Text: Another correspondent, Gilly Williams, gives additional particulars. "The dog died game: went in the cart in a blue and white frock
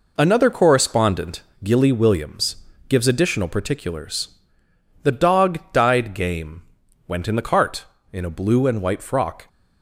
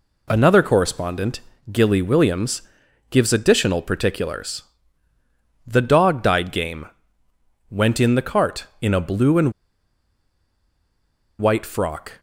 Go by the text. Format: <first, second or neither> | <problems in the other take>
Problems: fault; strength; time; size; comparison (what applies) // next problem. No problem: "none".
first | pauses between "and" and "white"; strong; at 9.5 s; 1.8 s long